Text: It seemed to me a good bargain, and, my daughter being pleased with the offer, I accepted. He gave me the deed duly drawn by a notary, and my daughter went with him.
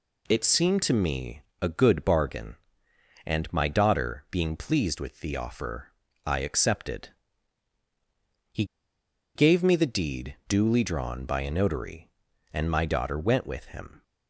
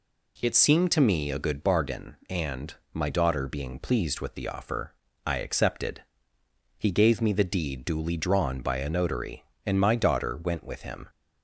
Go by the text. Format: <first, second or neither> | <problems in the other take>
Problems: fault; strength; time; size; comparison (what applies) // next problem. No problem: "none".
second | pauses between "me" and "a"; slight; at 1.4 s; 0.20 s long // pauses between "He" and "gave"; noticeable; at 8.6 s; 0.71 s long